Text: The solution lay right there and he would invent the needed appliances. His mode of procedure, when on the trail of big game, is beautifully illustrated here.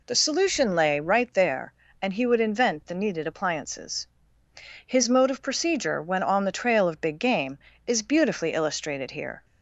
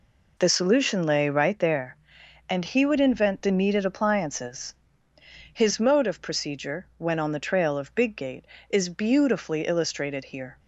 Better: first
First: none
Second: says "gate" for "game"; at 8.1 s

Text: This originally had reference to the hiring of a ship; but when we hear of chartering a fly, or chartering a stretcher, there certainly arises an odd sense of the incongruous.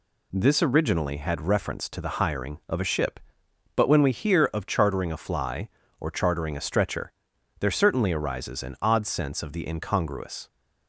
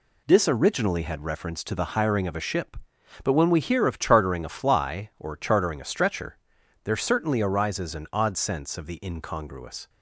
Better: neither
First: none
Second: none

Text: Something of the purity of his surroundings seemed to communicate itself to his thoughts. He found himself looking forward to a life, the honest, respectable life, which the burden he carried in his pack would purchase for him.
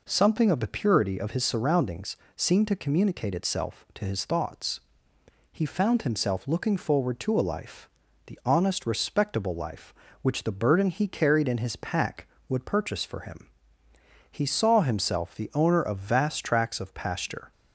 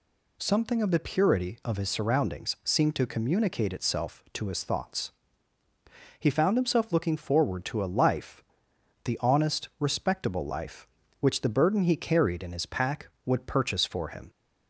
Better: second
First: pauses between "surroundings" and "seemed"; slight; at 2.1 s; 0.20 s long // goes on to say "He saw himself the owner of vast tracts of pasture"; strong; from 14.2 s on; 3.2 s long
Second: none

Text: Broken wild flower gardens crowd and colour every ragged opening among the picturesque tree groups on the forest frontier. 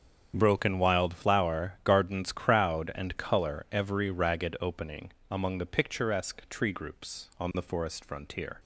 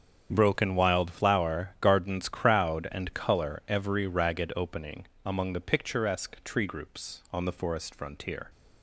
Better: neither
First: starts louder than the rest; strong; until 1.3 s; 8 dB // pauses between "opening" and "among"; slight; at 5.1 s; 0.18 s long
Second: starts louder than the rest; strong; until 1.3 s; 8 dB // pauses between "opening" and "among"; slight; at 5.0 s; 0.18 s long

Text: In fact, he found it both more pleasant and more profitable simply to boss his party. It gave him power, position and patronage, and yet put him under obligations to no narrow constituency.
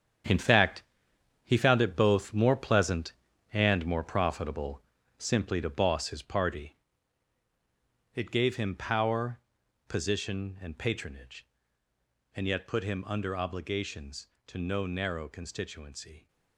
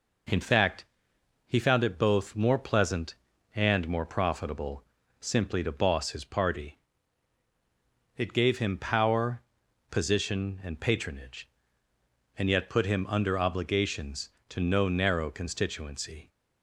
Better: second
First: gets quieter; strong; throughout; 10.5 dB // pauses between "profitable" and "simply"; at 4.8 s; 0.38 s long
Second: pauses between "profitable" and "simply"; at 4.8 s; 0.38 s long

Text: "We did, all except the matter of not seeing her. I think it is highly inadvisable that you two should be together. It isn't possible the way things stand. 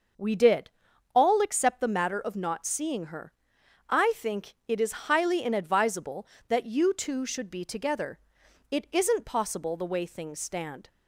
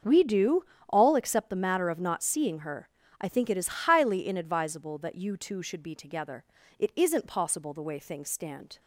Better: first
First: starts louder than the rest; noticeable; until 1.6 s; 6 dB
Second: starts louder than the rest; until 1.3 s; 6.5 dB // says "do" for "did"; at 0.2 s

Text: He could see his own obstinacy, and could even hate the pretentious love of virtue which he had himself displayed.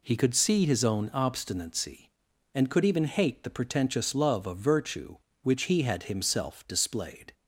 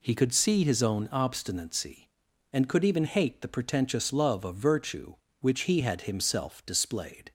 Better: neither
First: none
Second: none

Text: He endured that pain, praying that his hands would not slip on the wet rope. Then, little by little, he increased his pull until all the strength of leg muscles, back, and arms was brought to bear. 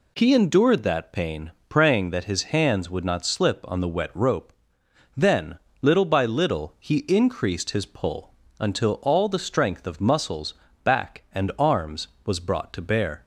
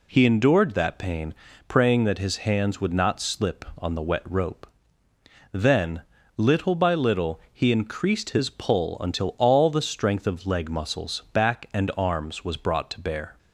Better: second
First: pauses between "pull" and "until"; slight; at 8.3 s; 0.28 s long // skips "leg"; at 9.9 s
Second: none

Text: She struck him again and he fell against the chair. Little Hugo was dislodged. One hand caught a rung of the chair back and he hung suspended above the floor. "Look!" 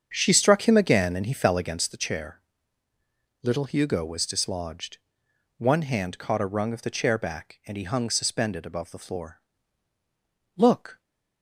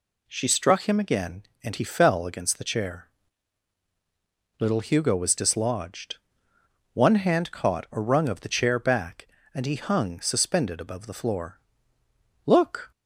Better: second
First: starts louder than the rest; strong; until 1.9 s; 7.5 dB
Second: none

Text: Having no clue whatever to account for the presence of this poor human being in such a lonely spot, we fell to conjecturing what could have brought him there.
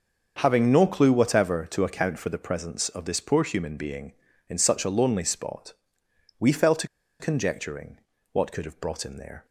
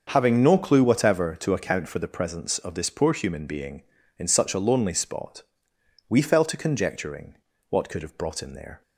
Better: second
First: starts louder than the rest; until 1.4 s; 6.5 dB // pauses between "to" and "conjecturing"; slight; at 6.8 s; 0.34 s long // pauses between "conjecturing" and "what"; slight; at 7.9 s; 0.36 s long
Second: starts louder than the rest; until 1.1 s; 6.5 dB // pauses between "conjecturing" and "what"; slight; at 7.3 s; 0.36 s long

